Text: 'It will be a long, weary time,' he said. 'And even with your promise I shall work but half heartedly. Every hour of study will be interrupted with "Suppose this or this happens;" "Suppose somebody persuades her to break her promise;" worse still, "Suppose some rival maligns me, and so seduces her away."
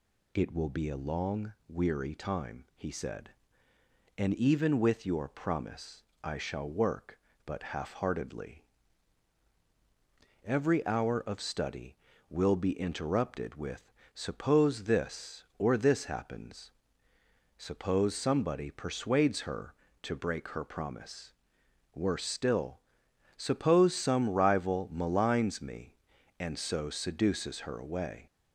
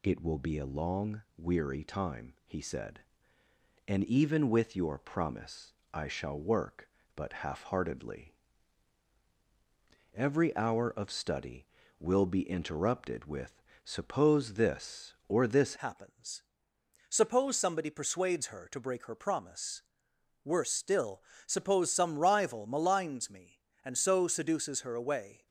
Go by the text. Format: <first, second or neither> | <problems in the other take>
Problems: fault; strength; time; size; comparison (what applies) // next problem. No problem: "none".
first | pauses between "promise" and "I"; slight; at 5.7 s; 0.20 s long; slight in the first // pauses between "with" and "Suppose"; slight; at 13.6 s; 0.24 s long; slight in the first // changes voice at "happens"; from 15.7 s on; 9.7 s long